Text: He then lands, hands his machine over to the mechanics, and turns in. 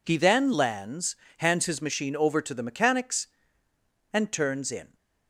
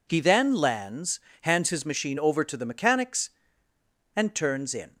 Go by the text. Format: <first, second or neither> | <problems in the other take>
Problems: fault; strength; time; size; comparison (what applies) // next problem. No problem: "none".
neither | none